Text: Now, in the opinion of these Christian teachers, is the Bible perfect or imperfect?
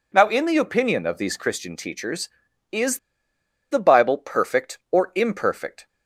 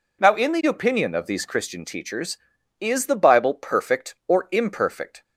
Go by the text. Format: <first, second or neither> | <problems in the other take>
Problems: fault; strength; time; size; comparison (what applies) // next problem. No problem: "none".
second | pauses between "is" and "the"; noticeable; at 2.9 s; 0.72 s long